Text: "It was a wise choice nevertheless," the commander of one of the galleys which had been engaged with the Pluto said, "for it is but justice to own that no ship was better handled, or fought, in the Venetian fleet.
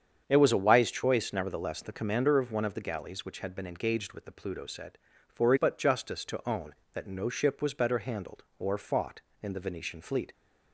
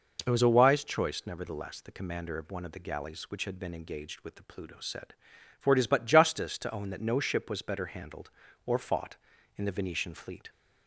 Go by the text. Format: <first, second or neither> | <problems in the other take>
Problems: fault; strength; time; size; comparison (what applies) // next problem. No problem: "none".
second | starts louder than the rest; strong; until 1.2 s; 7.5 dB // skips "is"; at 5.5 s